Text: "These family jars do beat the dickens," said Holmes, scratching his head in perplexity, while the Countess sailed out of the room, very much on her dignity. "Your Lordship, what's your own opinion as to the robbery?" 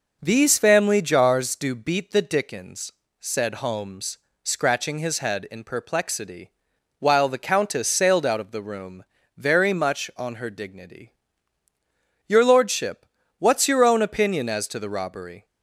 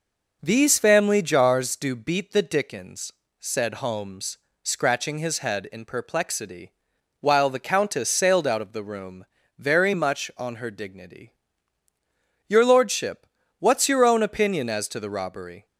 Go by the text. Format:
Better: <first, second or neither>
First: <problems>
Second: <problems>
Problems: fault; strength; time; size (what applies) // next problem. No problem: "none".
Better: neither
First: none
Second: none